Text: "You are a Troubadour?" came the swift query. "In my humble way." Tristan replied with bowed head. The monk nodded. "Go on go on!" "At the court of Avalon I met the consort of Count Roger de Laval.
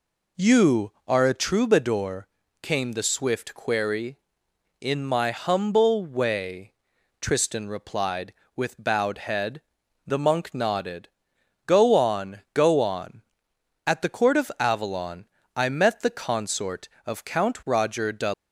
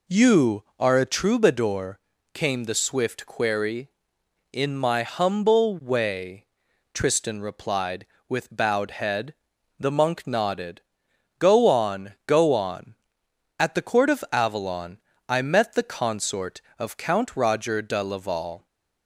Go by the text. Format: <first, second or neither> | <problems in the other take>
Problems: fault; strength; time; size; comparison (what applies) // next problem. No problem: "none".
second | pauses between "Avalon" and "I"; slight; at 15.2 s; 0.30 s long; slight in the second // stops before "Laval"; at 18.3 s